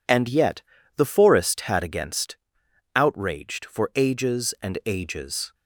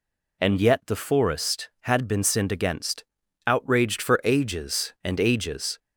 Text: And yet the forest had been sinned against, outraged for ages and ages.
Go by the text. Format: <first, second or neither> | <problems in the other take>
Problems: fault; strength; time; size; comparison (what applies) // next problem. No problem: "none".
second | pauses between "yet" and "the"; slight; at 0.6 s; 0.34 s long // skips "been sinned"; at 1.8 s